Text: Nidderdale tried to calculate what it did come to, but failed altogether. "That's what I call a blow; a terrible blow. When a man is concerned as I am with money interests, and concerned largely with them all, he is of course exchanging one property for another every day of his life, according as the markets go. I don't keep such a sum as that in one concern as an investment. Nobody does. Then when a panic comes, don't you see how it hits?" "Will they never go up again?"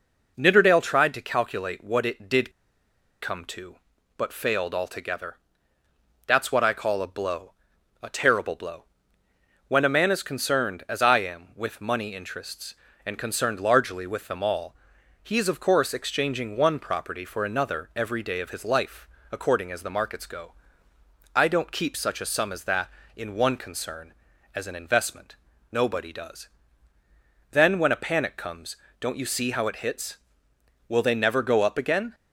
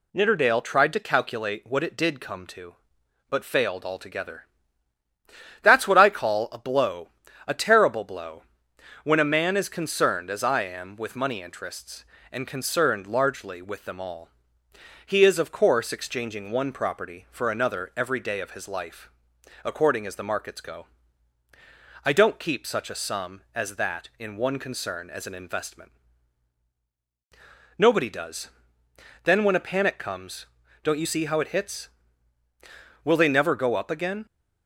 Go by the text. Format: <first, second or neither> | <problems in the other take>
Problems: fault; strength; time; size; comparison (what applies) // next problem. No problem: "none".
second | pauses between "did" and "come"; noticeable; at 2.5 s; 0.71 s long